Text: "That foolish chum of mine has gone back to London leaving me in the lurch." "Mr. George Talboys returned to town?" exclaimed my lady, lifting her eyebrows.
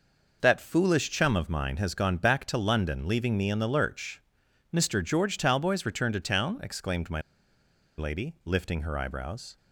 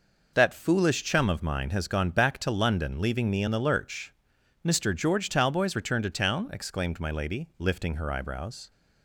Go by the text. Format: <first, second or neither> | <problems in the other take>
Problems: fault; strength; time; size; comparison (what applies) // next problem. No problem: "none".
second | pauses between "my" and "lady"; noticeable; at 7.1 s; 0.77 s long